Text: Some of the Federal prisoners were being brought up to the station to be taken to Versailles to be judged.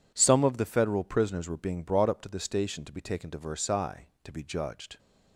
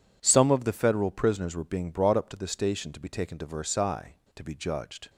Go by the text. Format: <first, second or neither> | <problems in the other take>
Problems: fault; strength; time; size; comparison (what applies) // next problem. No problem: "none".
neither | none